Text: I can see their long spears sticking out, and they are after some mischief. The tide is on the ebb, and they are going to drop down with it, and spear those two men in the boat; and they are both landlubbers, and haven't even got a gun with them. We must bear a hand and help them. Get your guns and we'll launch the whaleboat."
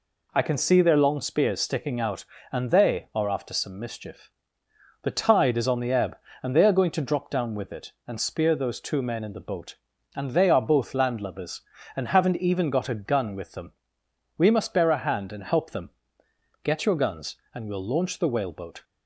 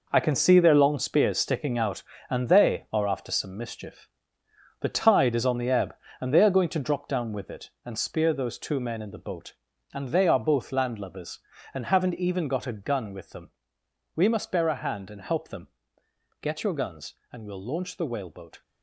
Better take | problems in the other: first | gets quieter; strong; throughout; 10 dB

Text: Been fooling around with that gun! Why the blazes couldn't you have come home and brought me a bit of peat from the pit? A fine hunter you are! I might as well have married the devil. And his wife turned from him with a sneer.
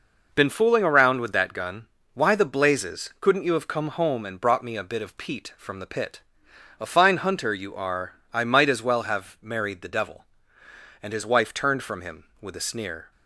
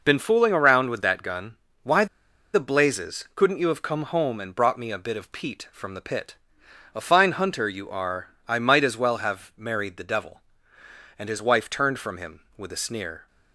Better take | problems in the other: first | pauses between "Why" and "the"; noticeable; at 2.0 s; 0.48 s long

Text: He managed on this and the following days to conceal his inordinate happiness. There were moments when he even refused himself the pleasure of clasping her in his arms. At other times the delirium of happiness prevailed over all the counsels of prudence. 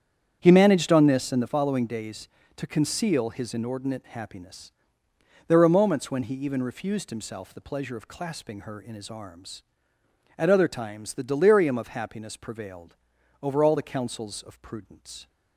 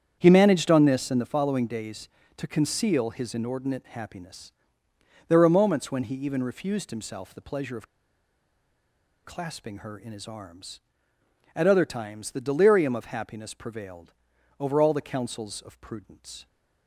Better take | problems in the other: first | starts louder than the rest; strong; until 1.2 s; 8.5 dB; strong in the first // pauses between "of" and "clasping"; strong; at 7.8 s; 1.3 s long // pauses between "prevailed" and "over"; noticeable; at 14.1 s; 0.48 s long; noticeable in the first

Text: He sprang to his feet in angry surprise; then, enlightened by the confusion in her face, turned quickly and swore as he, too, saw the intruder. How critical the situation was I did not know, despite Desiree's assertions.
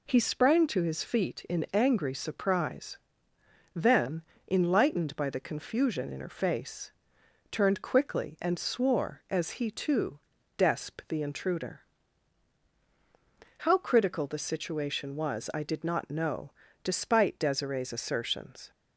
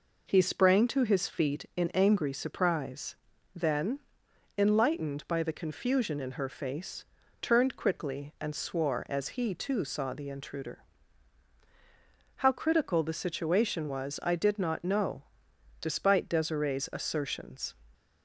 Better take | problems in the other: second | says "desp" for "saw"; at 10.5 s

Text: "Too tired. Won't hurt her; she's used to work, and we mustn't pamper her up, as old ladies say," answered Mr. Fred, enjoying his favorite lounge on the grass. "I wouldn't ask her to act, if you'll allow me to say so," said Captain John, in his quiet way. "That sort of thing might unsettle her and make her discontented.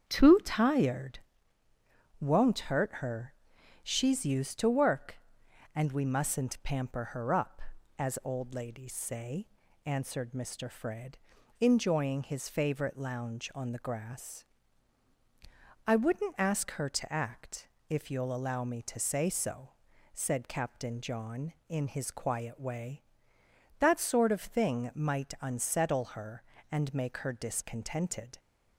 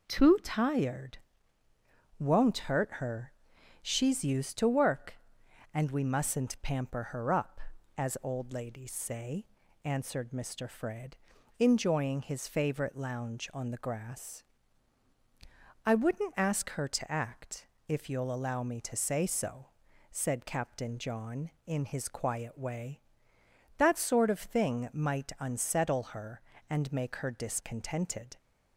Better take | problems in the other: second | starts louder than the rest; strong; until 1.3 s; 8 dB

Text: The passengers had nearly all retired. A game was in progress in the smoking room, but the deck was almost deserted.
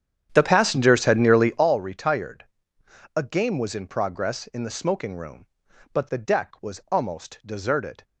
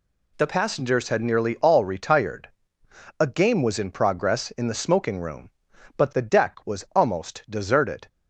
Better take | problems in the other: second | starts louder than the rest; strong; until 1.7 s; 9.5 dB

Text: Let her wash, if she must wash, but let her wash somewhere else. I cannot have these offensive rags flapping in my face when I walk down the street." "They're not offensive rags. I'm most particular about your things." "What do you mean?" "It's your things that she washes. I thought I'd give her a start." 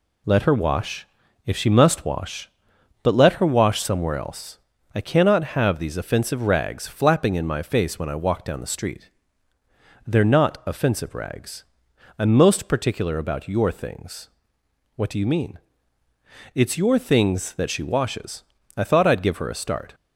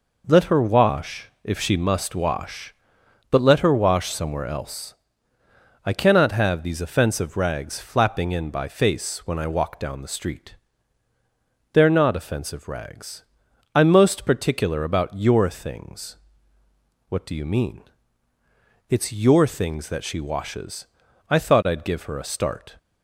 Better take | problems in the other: first | says "by" for "my"; at 8.4 s

